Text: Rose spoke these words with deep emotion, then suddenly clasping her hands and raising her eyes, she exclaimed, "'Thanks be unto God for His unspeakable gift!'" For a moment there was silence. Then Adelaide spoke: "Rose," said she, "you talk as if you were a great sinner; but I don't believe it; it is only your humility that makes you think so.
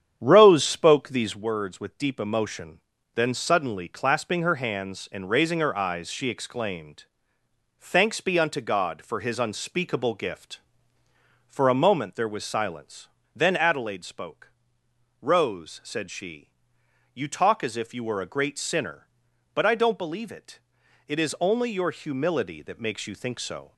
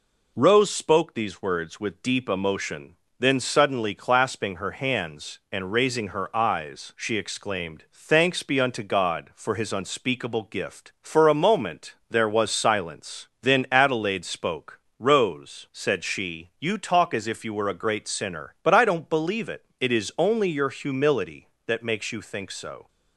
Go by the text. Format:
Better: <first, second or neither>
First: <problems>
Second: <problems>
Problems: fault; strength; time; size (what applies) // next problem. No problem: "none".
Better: second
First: starts louder than the rest; strong; until 1.5 s; 9 dB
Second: none